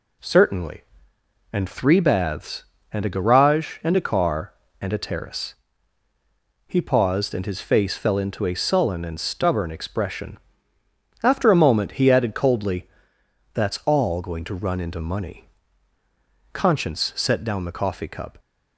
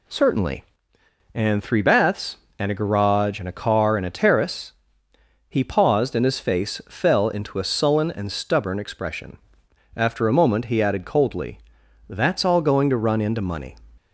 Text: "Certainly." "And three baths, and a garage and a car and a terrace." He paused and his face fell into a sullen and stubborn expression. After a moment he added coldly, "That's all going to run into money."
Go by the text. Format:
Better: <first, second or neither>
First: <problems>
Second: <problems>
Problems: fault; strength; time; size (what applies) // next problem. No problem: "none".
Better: second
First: goes on to say "Conscience set down the coffee cup"; strong; from 16.5 s on; 1.8 s long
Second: none